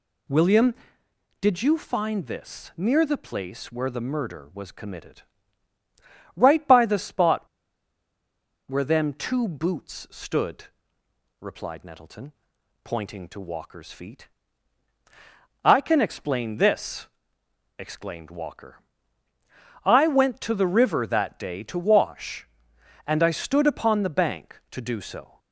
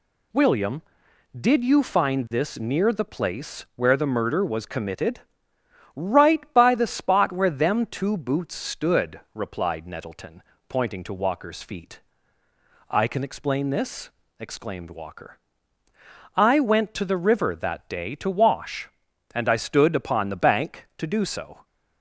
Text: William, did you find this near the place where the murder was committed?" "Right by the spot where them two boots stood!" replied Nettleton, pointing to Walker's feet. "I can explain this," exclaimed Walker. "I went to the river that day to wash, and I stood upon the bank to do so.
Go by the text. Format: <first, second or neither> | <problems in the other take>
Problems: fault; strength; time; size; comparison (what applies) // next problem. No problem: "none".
second | pauses between "spot" and "where"; at 7.4 s; 1.2 s long